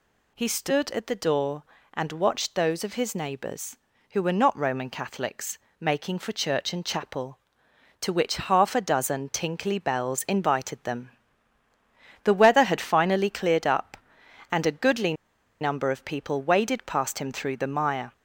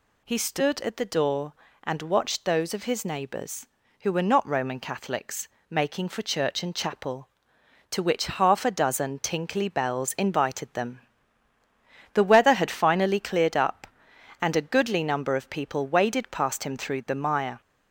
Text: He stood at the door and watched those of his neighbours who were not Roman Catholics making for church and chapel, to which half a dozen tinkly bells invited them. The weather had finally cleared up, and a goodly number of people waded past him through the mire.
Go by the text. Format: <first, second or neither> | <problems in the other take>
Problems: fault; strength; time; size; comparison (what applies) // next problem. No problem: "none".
second | pauses between "Catholics" and "making"; slight; at 5.5 s; 0.22 s long; slight in the second // pauses between "goodly" and "number"; noticeable; at 15.1 s; 0.47 s long